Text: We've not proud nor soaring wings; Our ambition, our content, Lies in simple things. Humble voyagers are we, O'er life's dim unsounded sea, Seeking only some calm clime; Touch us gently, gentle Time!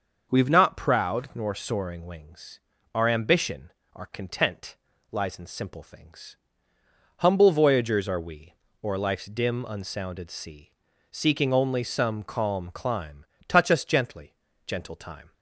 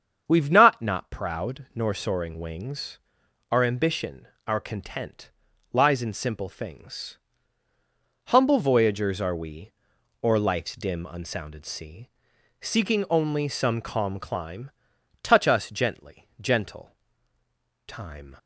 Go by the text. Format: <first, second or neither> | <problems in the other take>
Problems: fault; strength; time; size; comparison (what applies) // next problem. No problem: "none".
first | starts louder than the rest; strong; until 1.2 s; 7.5 dB; noticeable in the first // says "not" twice; at 0.8 s // pauses between "gentle" and "Time"; noticeable; at 16.9 s; 0.92 s long